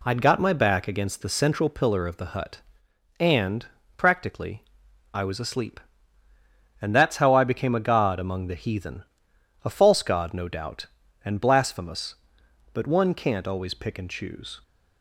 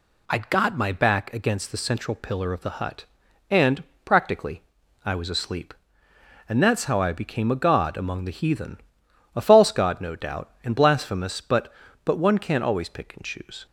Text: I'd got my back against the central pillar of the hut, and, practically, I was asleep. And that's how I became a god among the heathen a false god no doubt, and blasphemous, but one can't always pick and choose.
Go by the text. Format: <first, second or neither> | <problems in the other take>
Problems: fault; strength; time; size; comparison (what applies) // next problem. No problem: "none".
first | pauses between "heathen" and "a"; noticeable; at 8.7 s; 0.60 s long; noticeable in the first // says "but" twice; at 12.0 s